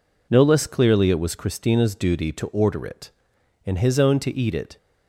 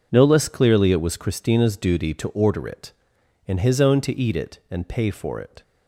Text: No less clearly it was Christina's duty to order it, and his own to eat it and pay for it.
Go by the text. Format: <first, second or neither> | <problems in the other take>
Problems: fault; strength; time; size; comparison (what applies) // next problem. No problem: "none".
second | stops before "and pay for it"; at 4.7 s